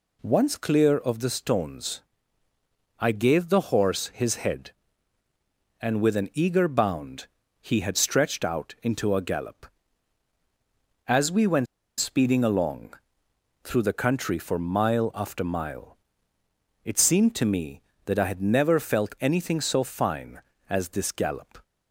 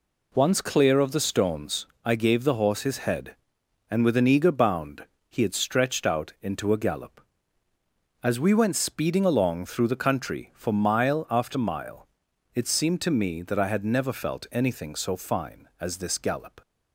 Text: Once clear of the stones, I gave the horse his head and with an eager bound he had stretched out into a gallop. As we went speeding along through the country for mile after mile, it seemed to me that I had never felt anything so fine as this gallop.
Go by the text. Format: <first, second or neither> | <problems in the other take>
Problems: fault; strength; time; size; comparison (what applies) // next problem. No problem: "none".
second | pauses between "bound" and "he"; slight; at 7.2 s; 0.34 s long; slight in the second // pauses between "went" and "speeding"; slight; at 11.6 s; 0.34 s long // pauses between "along" and "through"; noticeable; at 12.9 s; 0.68 s long